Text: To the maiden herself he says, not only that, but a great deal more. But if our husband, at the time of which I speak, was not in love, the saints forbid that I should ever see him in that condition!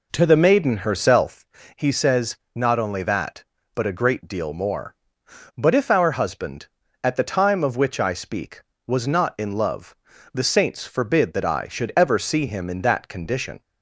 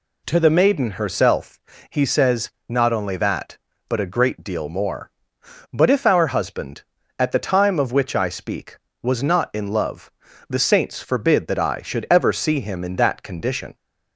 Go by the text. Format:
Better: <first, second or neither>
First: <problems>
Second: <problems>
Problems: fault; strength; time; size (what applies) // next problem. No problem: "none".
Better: second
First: starts louder than the rest; until 1.4 s; 4 dB // pauses between "herself" and "he"; slight; at 1.4 s; 0.30 s long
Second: pauses between "herself" and "he"; slight; at 1.6 s; 0.30 s long